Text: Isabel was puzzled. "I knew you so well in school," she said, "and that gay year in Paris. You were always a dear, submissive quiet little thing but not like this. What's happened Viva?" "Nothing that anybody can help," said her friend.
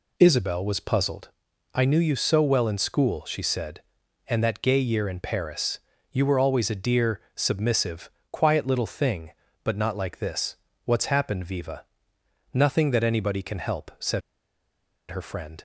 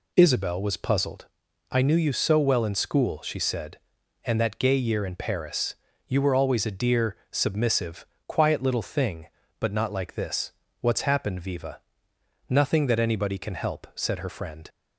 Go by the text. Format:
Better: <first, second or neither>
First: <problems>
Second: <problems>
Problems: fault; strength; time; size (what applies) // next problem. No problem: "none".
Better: second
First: pauses between "submissive" and "quiet"; slight; at 8.1 s; 0.22 s long // pauses between "said" and "her"; noticeable; at 14.2 s; 0.88 s long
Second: pauses between "submissive" and "quiet"; slight; at 8.0 s; 0.22 s long